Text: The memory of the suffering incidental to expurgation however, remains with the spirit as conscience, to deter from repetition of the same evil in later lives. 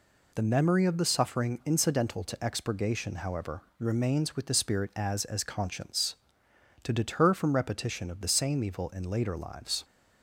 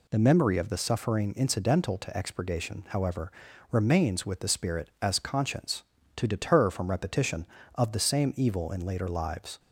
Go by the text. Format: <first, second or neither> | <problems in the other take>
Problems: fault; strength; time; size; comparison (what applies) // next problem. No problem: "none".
second | says "as" twice; at 5.2 s